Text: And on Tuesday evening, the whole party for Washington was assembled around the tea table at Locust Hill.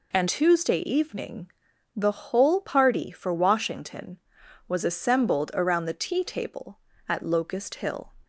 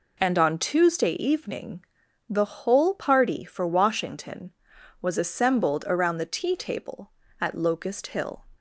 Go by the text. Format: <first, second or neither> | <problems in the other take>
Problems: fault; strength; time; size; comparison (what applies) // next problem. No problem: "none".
second | skips "on"; at 0.2 s